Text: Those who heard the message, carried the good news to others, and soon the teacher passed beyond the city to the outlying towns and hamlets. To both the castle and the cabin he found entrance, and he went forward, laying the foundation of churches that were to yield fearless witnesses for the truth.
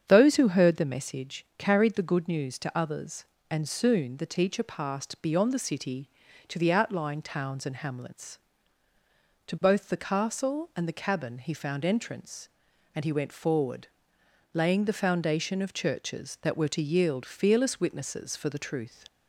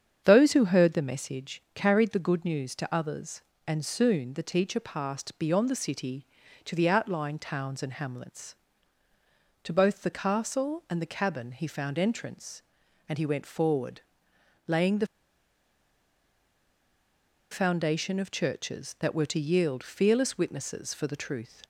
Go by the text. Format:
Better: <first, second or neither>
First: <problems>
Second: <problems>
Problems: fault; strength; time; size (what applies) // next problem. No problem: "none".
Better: first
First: starts louder than the rest; strong; until 1.0 s; 8 dB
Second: starts louder than the rest; strong; until 1.2 s; 8 dB // pauses between "the" and "foundation"; strong; at 15.0 s; 2.4 s long